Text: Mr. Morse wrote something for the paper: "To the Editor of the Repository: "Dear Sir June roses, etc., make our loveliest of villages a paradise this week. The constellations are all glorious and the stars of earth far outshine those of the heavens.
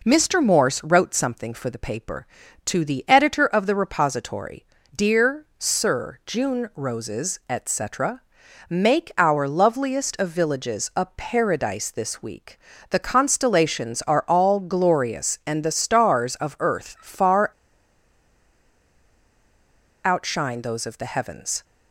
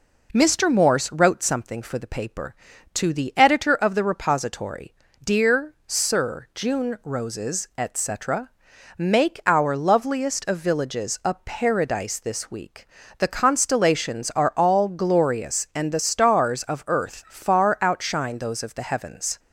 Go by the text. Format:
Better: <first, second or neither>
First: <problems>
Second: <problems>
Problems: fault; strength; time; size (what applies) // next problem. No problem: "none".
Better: second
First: pauses between "Dear" and "Sir"; slight; at 5.4 s; 0.16 s long // pauses between "far" and "outshine"; strong; at 17.4 s; 2.5 s long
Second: pauses between "Dear" and "Sir"; slight; at 5.7 s; 0.16 s long